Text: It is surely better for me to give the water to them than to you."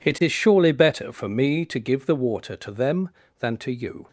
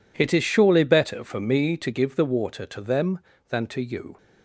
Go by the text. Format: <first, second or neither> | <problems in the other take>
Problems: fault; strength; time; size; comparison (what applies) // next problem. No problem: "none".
neither | none